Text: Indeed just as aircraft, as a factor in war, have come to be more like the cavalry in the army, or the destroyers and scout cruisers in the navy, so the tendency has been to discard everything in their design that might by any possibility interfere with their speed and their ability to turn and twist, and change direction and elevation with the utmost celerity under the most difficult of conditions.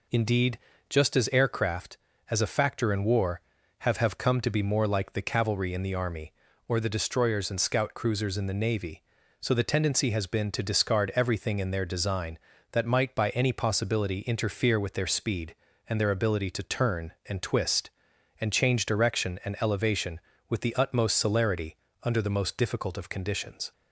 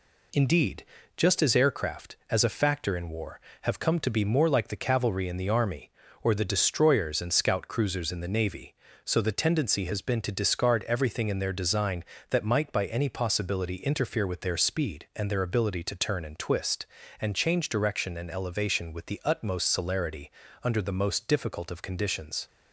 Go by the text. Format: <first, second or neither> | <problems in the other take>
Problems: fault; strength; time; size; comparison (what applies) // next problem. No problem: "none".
second | pauses between "Indeed" and "just"; slight; at 0.5 s; 0.30 s long; slight in the second // says "have" twice; at 3.9 s // pauses between "celerity" and "under"; slight; at 21.7 s; 0.28 s long; slight in the second